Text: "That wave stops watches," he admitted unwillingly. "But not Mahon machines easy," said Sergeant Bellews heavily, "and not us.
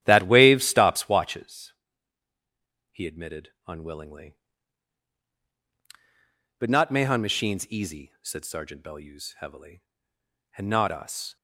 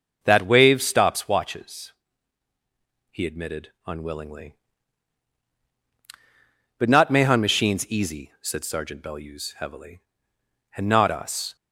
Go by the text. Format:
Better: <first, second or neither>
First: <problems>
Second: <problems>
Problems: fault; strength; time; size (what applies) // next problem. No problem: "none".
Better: second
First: starts louder than the rest; strong; until 1.5 s; 11 dB // pauses between "admitted" and "unwillingly"; slight; at 3.5 s; 0.16 s long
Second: pauses between "admitted" and "unwillingly"; slight; at 3.7 s; 0.16 s long